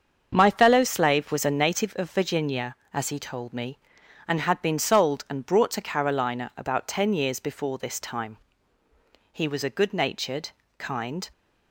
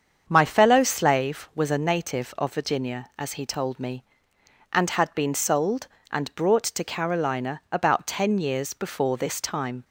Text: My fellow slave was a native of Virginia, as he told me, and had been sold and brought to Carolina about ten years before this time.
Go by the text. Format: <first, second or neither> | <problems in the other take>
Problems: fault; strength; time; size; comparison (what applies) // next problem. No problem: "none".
second | starts louder than the rest; until 1.3 s; 7 dB; strong in the second // goes on to say "He was a good natured kind"; strong; from 9.3 s on; 1.9 s long